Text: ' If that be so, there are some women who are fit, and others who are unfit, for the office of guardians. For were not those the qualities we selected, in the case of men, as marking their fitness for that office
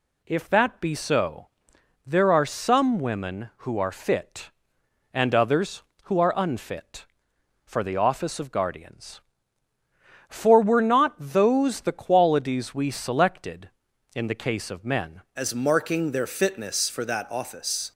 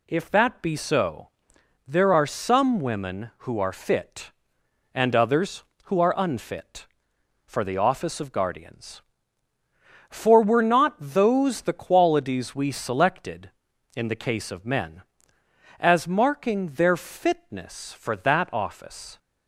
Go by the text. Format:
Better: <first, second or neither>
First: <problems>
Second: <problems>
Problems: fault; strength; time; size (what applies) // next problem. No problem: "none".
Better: second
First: changes voice at "as"; from 15.3 s on; 2.6 s long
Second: none